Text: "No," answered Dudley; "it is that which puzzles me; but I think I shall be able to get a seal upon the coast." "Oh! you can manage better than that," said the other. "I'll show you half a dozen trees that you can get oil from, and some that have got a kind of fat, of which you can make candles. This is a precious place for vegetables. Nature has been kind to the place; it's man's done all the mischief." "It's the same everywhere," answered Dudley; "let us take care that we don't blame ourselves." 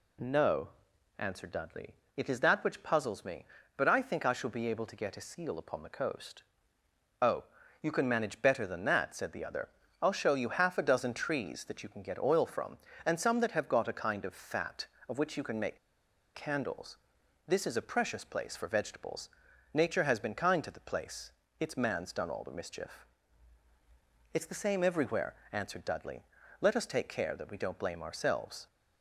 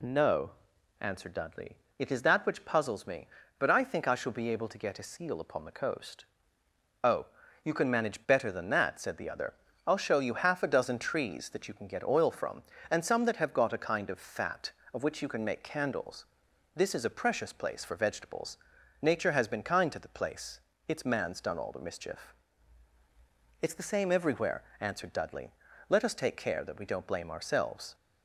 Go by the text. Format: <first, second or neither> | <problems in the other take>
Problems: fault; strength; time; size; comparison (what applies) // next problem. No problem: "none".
second | pauses between "make" and "candles"; noticeable; at 15.7 s; 0.57 s long